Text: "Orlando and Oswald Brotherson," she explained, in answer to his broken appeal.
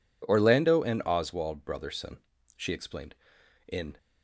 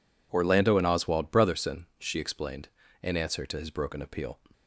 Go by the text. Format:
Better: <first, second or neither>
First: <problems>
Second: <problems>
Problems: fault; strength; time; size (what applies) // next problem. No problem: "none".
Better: second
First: stops before "answer to his broken appeal"; at 3.9 s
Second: none